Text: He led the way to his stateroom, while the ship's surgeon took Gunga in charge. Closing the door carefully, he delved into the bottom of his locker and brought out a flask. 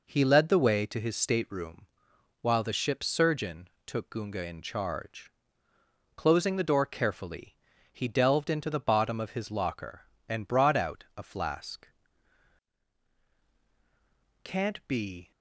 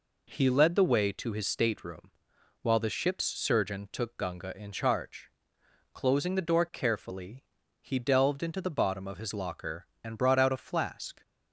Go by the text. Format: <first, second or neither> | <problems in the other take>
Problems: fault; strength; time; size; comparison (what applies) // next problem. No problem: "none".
second | pauses between "surgeon" and "took"; slight; at 3.6 s; 0.16 s long // goes on to say "Can't be"; noticeable; from 14.4 s on; 0.88 s long